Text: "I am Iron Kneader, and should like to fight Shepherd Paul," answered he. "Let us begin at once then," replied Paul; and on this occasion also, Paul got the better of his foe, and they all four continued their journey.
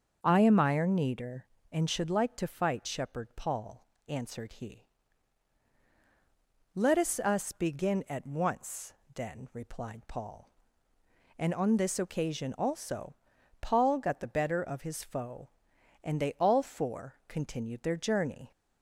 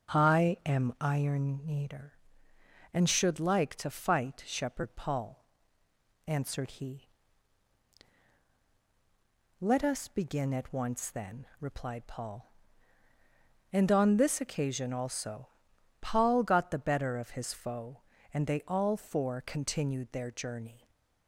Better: second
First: starts louder than the rest; until 1.2 s; 6.5 dB // says "us" twice; at 7.1 s // pauses between "once" and "then"; slight; at 8.9 s; 0.22 s long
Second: starts louder than the rest; strong; until 1.2 s; 7.5 dB

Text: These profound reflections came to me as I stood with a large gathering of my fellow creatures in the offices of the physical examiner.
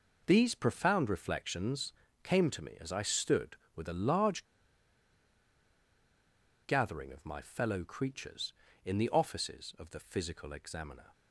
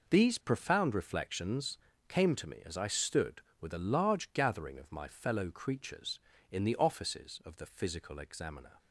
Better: second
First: pauses between "reflections" and "came"; slight; at 1.9 s; 0.32 s long // pauses between "large" and "gathering"; strong; at 4.4 s; 2.1 s long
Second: pauses between "reflections" and "came"; slight; at 1.7 s; 0.32 s long

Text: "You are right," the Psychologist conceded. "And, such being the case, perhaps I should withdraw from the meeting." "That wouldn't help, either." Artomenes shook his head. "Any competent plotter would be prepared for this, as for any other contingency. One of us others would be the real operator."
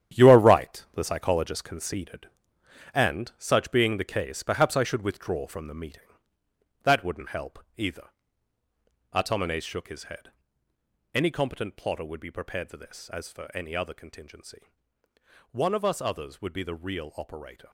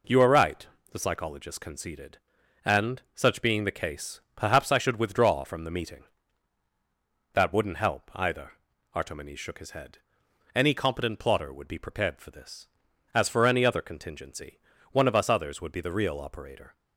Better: second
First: gets quieter; strong; throughout; 10 dB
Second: none

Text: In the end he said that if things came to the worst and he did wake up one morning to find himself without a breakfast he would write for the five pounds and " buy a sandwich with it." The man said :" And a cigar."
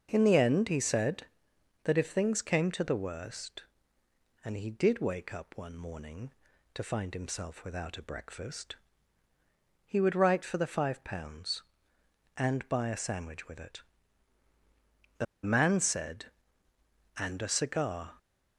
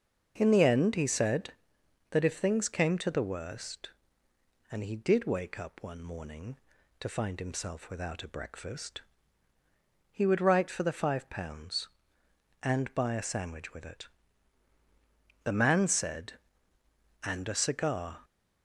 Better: second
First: starts louder than the rest; until 1.1 s; 6 dB // pauses between "breakfast" and "he"; at 8.7 s; 1.1 s long // pauses between "The" and "man"; slight; at 15.2 s; 0.20 s long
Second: starts louder than the rest; until 1.3 s; 6 dB // pauses between "breakfast" and "he"; at 9.0 s; 1.1 s long

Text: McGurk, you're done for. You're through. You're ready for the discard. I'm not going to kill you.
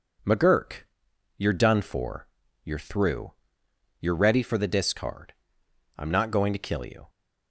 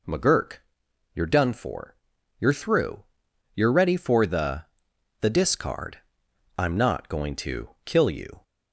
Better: first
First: none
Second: says "the" twice; at 5.2 s // pauses between "to" and "kill"; slight; at 7.6 s; 0.16 s long

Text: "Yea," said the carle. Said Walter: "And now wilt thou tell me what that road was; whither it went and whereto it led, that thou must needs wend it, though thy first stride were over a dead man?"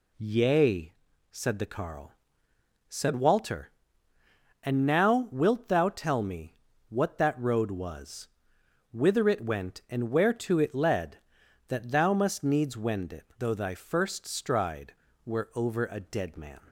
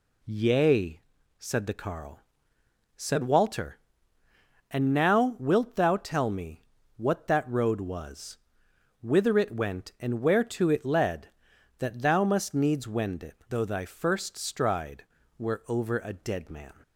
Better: neither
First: pauses between "me" and "what"; slight; at 6.5 s; 0.34 s long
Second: pauses between "me" and "what"; slight; at 6.6 s; 0.34 s long

